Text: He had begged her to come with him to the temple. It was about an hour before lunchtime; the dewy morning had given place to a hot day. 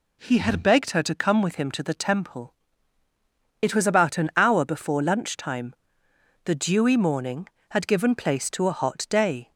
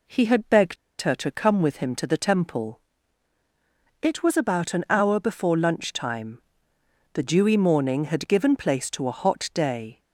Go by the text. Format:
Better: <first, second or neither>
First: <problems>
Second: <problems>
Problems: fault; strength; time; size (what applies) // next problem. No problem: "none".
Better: first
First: none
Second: pauses between "begged" and "her"; slight; at 0.7 s; 0.25 s long